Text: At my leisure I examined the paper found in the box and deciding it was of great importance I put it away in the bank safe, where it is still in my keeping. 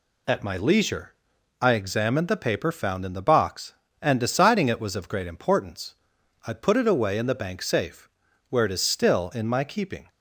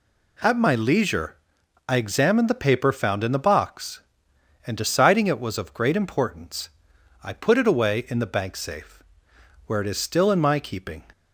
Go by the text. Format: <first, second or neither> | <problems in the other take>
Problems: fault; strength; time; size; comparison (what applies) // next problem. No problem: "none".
neither | pauses between "leisure" and "I"; noticeable; the same in both // pauses between "importance" and "I"; noticeable; the same in both